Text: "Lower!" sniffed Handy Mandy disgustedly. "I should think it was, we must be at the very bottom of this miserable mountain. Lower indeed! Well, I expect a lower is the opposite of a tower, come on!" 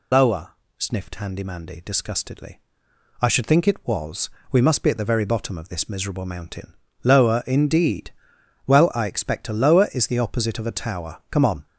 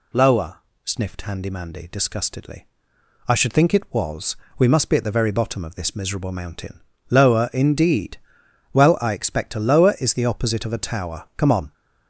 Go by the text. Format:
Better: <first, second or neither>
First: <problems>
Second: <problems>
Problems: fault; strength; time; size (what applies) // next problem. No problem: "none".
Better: second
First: loses the start of "Lower"; at 0.1 s; 45 ms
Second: none